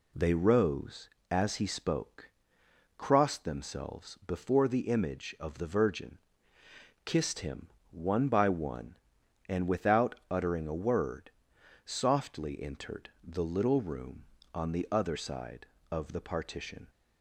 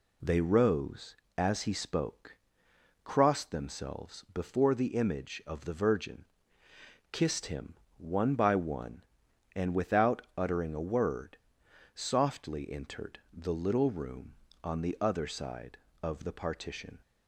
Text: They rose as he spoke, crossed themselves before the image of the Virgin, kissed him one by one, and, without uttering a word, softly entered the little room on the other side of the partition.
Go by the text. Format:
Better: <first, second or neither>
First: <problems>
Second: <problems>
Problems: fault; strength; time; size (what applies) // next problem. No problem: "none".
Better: neither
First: pauses between "him" and "one"; slight; at 7.6 s; 0.24 s long // pauses between "without" and "uttering"; slight; at 10.1 s; 0.16 s long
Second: pauses between "him" and "one"; slight; at 7.7 s; 0.24 s long // pauses between "without" and "uttering"; slight; at 10.2 s; 0.16 s long